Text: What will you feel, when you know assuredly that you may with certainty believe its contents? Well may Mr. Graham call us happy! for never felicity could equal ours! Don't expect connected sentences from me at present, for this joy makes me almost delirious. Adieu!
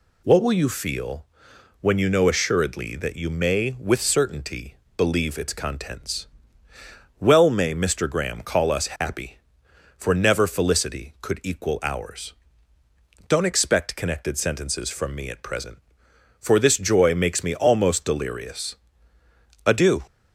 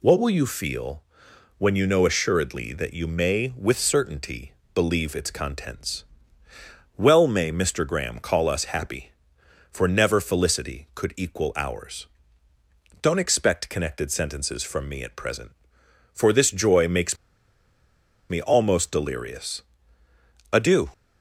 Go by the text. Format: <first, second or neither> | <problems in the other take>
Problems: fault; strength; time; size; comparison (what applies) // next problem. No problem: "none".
first | pauses between "certainty" and "believe"; slight; at 4.5 s; 0.20 s long; slight in the first // pauses between "makes" and "me"; at 17.1 s; 1.1 s long